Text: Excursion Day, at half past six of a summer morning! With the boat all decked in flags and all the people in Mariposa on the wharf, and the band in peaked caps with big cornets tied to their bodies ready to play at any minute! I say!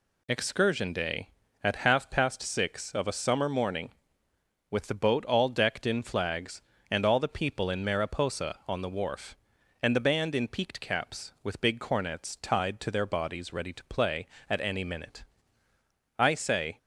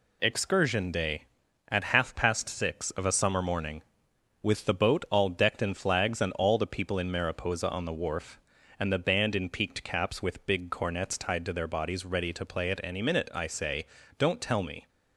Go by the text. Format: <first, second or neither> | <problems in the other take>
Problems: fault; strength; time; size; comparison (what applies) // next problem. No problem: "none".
first | goes on to say "Don't tell me"; noticeable; from 14.1 s on; 0.70 s long